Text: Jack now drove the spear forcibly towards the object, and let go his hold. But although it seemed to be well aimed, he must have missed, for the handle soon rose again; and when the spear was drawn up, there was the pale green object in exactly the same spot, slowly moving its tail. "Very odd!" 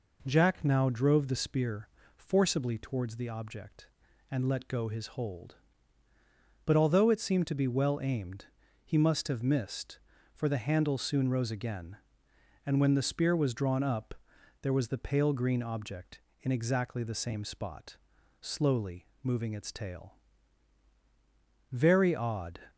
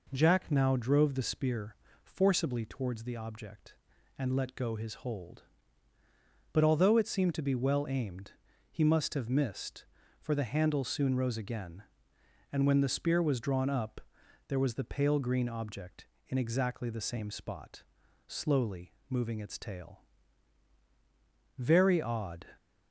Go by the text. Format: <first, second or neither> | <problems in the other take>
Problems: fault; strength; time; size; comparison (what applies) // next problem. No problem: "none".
neither | pauses between "spear" and "forcibly"; slight; the same in both // pauses between "slowly" and "moving"; slight; the same in both